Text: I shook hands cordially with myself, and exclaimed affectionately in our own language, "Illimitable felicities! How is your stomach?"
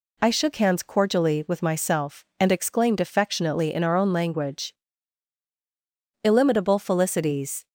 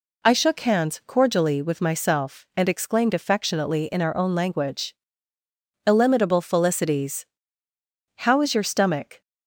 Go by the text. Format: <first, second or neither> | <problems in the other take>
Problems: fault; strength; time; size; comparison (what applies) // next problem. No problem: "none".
second | stops before "How is your stomach"; at 7.6 s